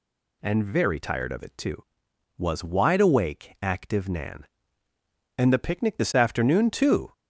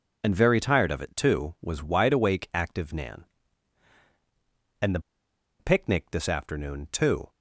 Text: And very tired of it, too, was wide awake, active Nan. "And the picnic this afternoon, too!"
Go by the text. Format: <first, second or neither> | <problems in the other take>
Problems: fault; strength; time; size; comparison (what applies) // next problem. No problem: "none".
first | pauses between "the" and "picnic"; noticeable; at 4.9 s; 0.60 s long